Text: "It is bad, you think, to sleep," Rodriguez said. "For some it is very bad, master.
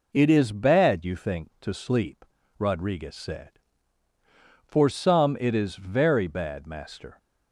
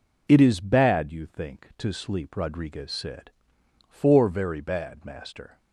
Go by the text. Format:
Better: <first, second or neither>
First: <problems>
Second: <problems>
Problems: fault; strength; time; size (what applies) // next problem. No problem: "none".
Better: first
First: none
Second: skips "some it is"; at 4.2 s